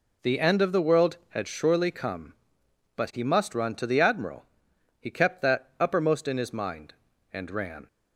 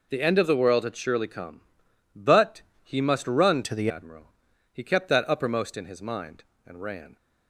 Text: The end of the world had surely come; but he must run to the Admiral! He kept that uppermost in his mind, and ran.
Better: first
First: none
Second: pauses between "but" and "he"; slight; at 2.6 s; 0.22 s long // changes voice from "to" to "the"; from 3.6 to 3.9 s; 0.3 s long

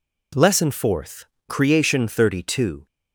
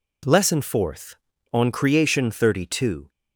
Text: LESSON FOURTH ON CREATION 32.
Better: second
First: skips "ON"; at 1.3 s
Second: none

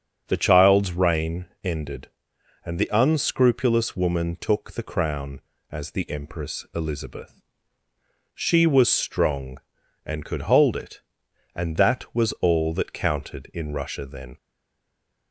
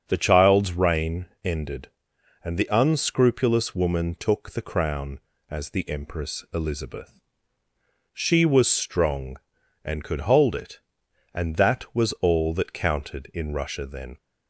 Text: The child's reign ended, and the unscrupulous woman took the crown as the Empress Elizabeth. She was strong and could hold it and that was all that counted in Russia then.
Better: second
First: starts louder than the rest; strong; until 1.2 s; 7 dB // pauses between "reign" and "ended"; slight; at 1.4 s; 0.20 s long // stays silent after the last word; slight; from 14.3 s on; 1.0 s long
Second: starts louder than the rest; strong; until 1.0 s; 7 dB // pauses between "reign" and "ended"; slight; at 1.2 s; 0.20 s long

